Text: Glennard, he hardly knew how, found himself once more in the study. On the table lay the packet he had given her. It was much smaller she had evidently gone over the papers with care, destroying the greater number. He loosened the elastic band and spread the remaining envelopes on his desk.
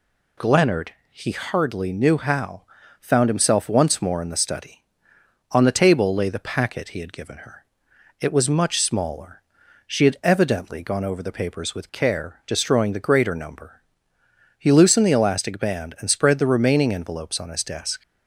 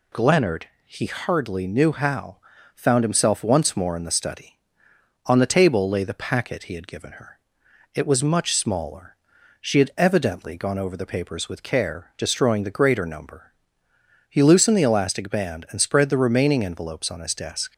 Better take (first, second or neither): neither